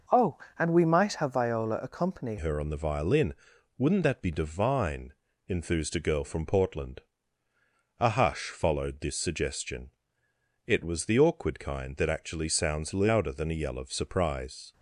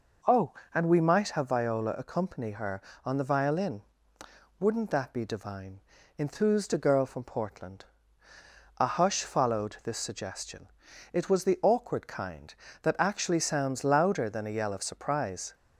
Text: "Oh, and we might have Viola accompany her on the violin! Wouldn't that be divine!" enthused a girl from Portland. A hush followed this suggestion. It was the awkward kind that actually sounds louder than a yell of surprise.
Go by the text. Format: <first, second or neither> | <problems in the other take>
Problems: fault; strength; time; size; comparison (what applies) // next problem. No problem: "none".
second | changes voice at "her"; from 2.3 s on; 12.4 s long